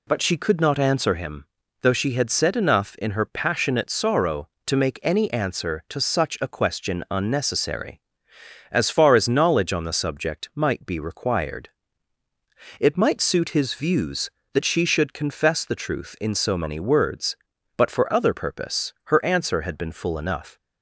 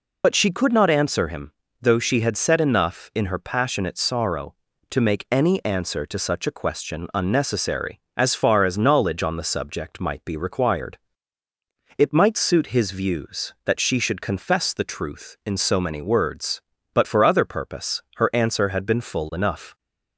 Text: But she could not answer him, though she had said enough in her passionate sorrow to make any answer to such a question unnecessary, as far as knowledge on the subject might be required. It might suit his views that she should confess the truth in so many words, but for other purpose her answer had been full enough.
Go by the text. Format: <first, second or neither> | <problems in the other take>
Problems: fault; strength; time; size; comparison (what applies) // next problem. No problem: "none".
first | loses the start of "But"; at 0.2 s; 50 ms